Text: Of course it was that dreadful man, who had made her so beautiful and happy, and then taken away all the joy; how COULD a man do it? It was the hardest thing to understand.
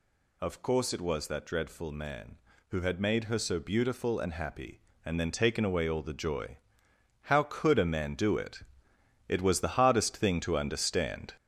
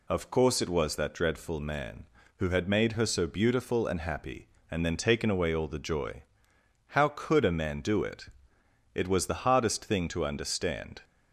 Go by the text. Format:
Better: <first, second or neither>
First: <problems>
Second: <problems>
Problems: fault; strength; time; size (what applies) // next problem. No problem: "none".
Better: second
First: gets louder; noticeable; throughout; 6 dB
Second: none